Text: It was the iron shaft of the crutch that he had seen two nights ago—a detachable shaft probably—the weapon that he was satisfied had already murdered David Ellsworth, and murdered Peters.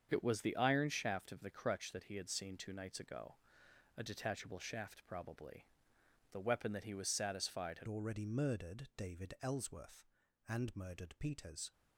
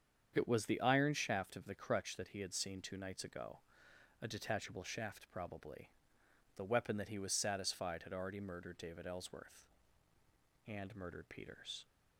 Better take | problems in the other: second | starts louder than the rest; strong; until 1.1 s; 7 dB; strong in the second // changes voice at "already"; from 7.8 s on; 3.9 s long

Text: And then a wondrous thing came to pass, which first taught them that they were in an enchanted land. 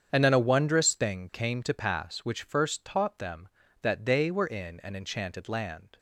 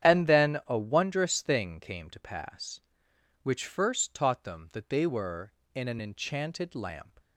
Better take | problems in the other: first | starts louder than the rest; strong; until 1.1 s; 9.5 dB; strong in the first // says "lamp" for "land"; at 6.7 s

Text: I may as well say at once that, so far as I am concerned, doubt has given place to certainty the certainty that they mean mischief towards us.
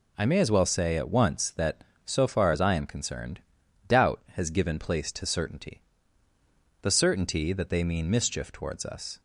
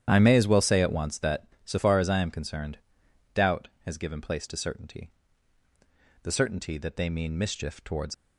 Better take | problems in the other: first | starts louder than the rest; strong; until 1.0 s; 10 dB // pauses between "certainty" and "the"; at 5.1 s; 1.1 s long; also in the first // stops before "us"; at 8.1 s

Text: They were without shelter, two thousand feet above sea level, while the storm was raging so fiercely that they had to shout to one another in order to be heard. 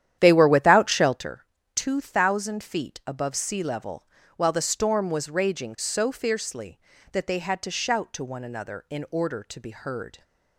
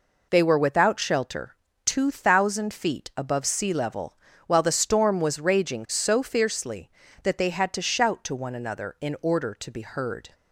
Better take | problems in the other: second | starts louder than the rest; strong; until 1.3 s; 10.5 dB

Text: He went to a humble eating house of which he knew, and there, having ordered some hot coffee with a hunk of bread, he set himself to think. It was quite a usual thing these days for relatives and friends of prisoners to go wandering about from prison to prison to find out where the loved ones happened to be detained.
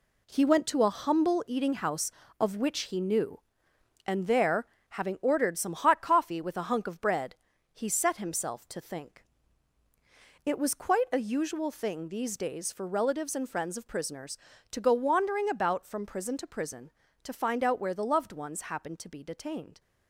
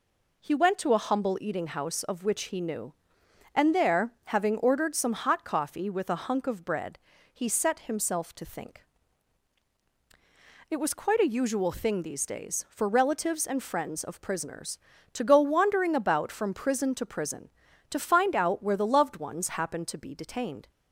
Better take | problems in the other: second | gets quieter; strong; throughout; 7.5 dB

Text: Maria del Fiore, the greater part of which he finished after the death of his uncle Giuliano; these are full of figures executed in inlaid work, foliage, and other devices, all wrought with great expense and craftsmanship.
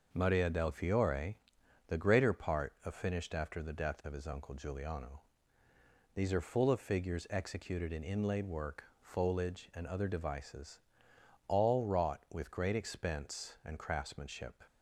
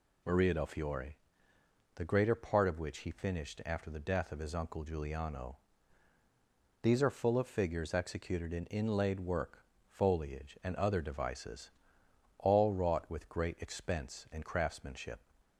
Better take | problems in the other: second | skips "which he"; at 2.9 s

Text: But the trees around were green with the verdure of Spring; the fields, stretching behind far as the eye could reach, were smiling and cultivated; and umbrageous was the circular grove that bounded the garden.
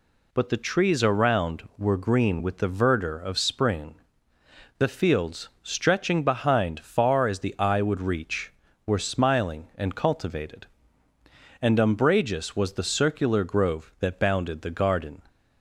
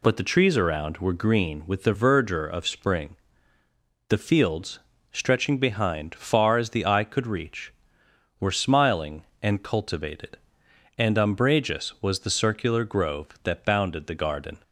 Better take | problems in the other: second | says "would" for "could"; at 7.8 s

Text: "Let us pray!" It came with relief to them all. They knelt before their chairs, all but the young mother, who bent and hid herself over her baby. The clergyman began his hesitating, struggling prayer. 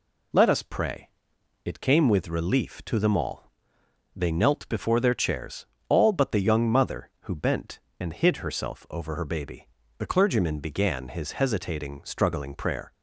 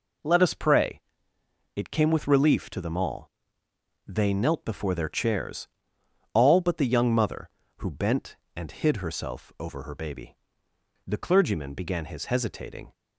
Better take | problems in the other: first | stops before "struggling prayer"; at 12.9 s

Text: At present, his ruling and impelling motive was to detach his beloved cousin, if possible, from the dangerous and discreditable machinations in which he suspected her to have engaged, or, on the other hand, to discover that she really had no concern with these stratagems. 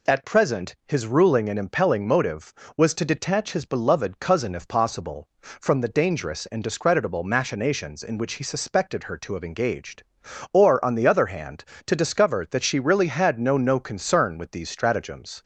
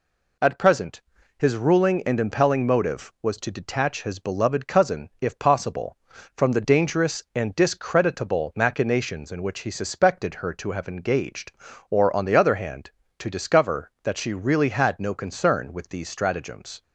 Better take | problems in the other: second | says "no" twice; at 13.5 s

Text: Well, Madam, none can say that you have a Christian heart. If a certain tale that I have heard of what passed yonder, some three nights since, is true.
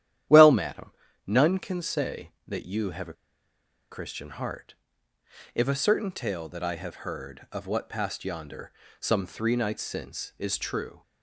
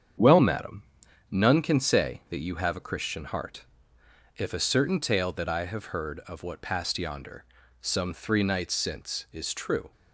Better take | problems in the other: second | starts louder than the rest; strong; until 1.6 s; 11.5 dB; strong in the second // pauses between "a" and "Christian"; noticeable; at 3.1 s; 0.78 s long

